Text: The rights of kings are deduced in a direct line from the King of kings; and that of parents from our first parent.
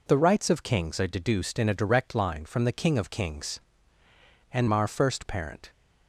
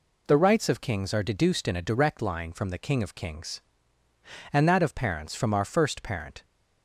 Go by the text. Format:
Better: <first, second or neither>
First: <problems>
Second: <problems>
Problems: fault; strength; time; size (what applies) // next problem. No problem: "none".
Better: second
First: skips "that of parents from"; at 4.6 s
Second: none